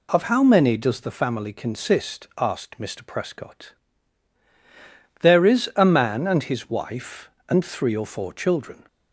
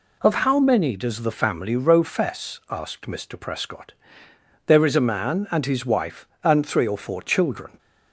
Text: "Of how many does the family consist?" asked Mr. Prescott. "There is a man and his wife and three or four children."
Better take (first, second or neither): first